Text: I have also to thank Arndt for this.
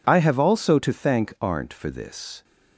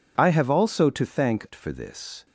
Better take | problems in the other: first | skips "Arndt"; at 1.4 s

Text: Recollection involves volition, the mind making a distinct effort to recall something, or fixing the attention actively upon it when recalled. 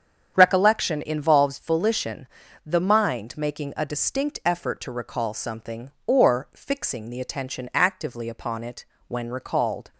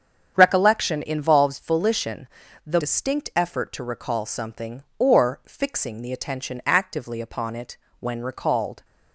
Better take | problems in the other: first | starts louder than the rest; strong; until 1.3 s; 8 dB; strong in the first // skips "mind making a"; at 2.7 s // pauses between "it" and "when"; slight; at 7.7 s; 0.22 s long; slight in the first

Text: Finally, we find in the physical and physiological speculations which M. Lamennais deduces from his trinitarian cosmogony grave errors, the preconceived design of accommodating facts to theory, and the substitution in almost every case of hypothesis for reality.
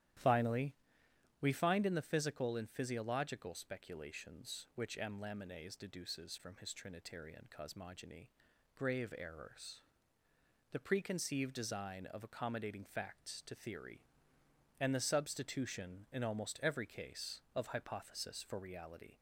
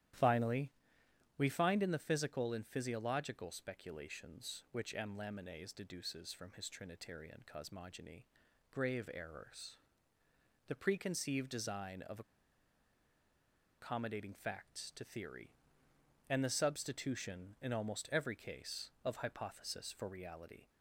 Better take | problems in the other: first | starts louder than the rest; strong; until 1.8 s; 12 dB; strong in the first // pauses between "cosmogony" and "grave"; noticeable; at 8.2 s; 0.46 s long; noticeable in the first // pauses between "of" and "accommodating"; strong; at 12.2 s; 1.5 s long

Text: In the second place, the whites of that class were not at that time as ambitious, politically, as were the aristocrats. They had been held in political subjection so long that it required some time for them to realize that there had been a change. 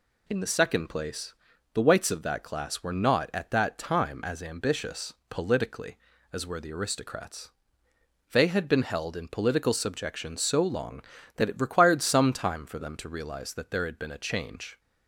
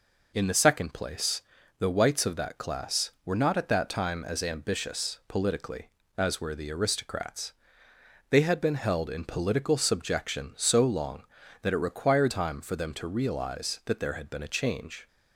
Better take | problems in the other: first | skips "some"; at 12.3 s

